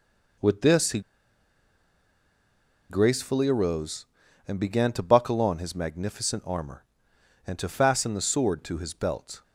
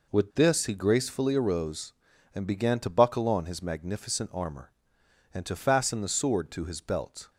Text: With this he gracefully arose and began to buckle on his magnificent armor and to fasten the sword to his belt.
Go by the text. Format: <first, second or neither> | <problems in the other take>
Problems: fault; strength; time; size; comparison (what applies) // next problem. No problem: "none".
second | pauses between "he" and "gracefully"; strong; at 0.9 s; 1.8 s long